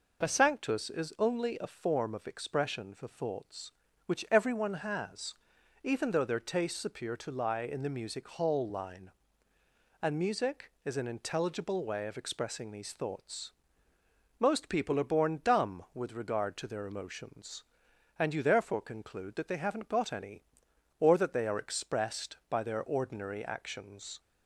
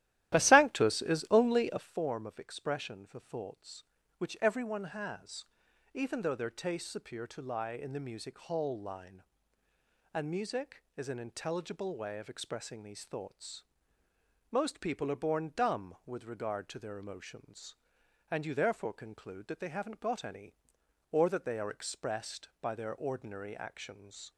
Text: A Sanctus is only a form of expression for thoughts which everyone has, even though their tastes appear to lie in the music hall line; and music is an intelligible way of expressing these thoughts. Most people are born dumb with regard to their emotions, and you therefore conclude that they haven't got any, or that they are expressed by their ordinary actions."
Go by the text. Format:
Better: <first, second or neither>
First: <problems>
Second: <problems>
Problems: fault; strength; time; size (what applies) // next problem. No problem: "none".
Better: first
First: none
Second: starts louder than the rest; strong; until 2.0 s; 14 dB